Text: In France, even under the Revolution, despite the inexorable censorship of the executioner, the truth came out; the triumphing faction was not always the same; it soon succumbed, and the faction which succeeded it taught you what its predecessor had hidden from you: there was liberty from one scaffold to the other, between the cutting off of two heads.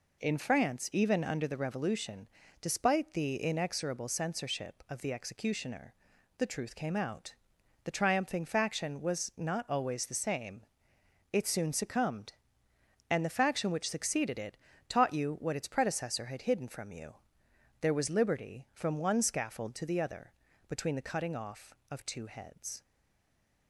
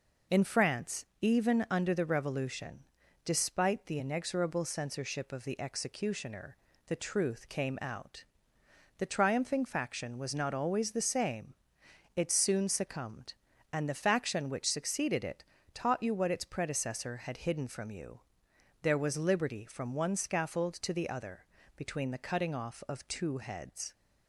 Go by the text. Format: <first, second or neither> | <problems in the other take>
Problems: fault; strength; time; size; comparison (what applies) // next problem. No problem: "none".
second | pauses between "it" and "taught"; slight; at 14.5 s; 0.32 s long; slight in the second // stays silent after the last word; slight; from 22.8 s on; 0.8 s long